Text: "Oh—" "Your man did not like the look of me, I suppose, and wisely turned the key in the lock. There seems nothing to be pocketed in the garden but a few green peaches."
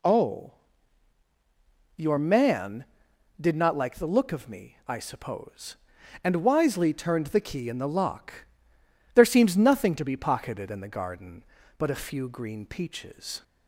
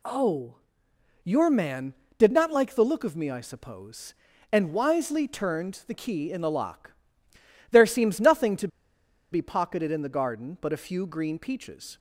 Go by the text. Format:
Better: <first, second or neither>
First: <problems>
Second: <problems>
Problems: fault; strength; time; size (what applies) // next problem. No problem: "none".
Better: first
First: none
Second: pauses between "to" and "be"; noticeable; at 8.6 s; 0.63 s long